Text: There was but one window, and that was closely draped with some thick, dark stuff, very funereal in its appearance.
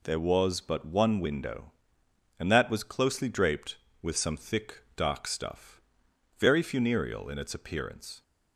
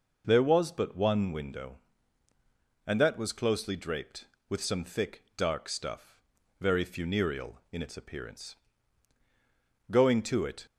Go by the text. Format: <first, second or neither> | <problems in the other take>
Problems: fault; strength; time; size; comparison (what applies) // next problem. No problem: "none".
first | goes on to say "Going to it"; noticeable; from 9.9 s on; 0.74 s long